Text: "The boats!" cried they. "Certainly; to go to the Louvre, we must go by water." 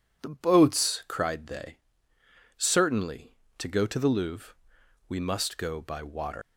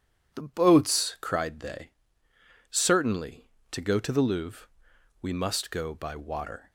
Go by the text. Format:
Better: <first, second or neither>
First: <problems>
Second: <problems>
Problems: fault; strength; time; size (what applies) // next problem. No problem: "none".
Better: second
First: leaves "water" unfinished; at 6.4 s; 155 ms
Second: none